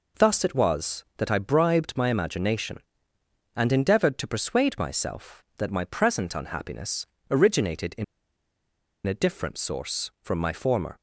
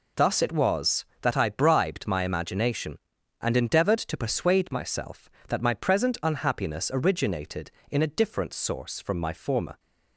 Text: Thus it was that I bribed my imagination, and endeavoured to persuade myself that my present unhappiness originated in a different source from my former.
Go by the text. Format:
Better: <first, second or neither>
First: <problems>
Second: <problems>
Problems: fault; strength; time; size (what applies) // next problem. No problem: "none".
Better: second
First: pauses between "unhappiness" and "originated"; slight; at 7.0 s; 0.26 s long // pauses between "in" and "a"; at 8.0 s; 1.0 s long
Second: none